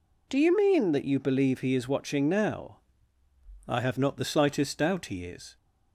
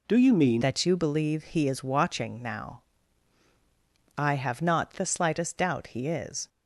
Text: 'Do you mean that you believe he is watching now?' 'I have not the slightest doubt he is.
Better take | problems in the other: first | changes voice at "that"; from 0.6 s on; 5.8 s long

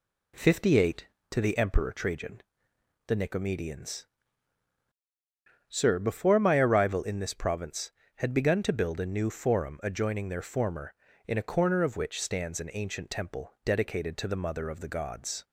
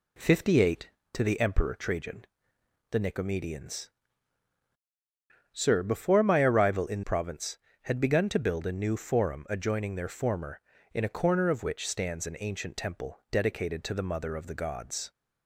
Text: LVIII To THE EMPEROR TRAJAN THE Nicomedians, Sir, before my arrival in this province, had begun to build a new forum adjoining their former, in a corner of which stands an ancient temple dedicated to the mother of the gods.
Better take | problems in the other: first | pauses between "TRAJAN" and "THE"; noticeable; at 2.2 s; 0.66 s long; noticeable in the first // skips "this"; at 7.0 s

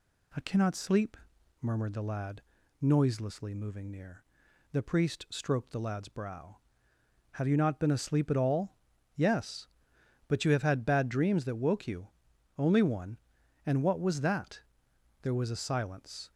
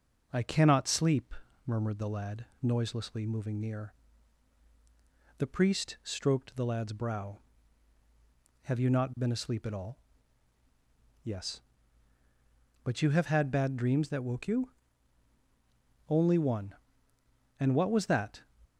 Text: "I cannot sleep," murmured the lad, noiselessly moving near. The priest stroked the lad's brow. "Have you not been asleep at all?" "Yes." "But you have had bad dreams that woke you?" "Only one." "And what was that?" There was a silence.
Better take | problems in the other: first | stops before "There was a silence"; at 18.6 s

